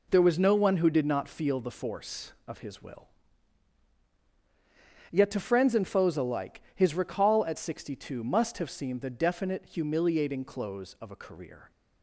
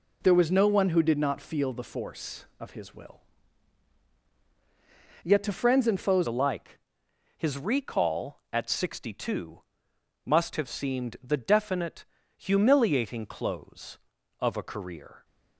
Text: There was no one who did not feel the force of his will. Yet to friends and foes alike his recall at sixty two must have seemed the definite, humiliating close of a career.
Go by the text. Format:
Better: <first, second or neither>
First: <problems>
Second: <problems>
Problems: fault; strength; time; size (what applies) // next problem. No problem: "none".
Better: first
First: none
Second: changes voice at "alike"; from 6.2 s on; 9.0 s long // pauses between "alike" and "his"; noticeable; at 6.7 s; 0.60 s long // pauses between "two" and "must"; noticeable; at 9.6 s; 0.60 s long